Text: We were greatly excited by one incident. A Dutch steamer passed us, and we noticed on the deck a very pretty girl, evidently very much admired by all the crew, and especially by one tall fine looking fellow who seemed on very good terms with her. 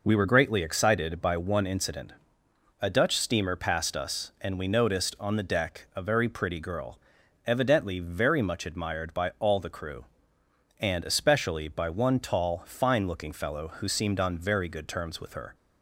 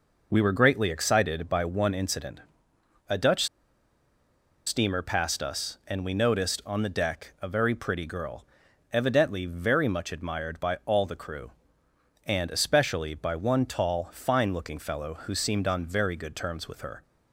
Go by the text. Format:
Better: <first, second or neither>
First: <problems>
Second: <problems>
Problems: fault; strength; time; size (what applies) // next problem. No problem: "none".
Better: first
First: none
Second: pauses between "Dutch" and "steamer"; at 3.4 s; 1.2 s long